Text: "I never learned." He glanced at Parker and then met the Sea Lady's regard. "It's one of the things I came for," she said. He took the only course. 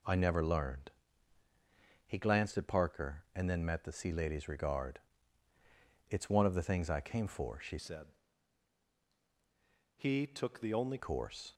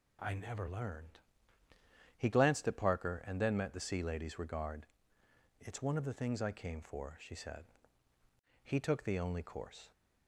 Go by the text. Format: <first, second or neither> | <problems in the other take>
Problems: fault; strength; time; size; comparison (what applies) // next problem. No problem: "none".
second | changes voice from "said" to "only"; from 7.7 to 10.9 s; 3.2 s long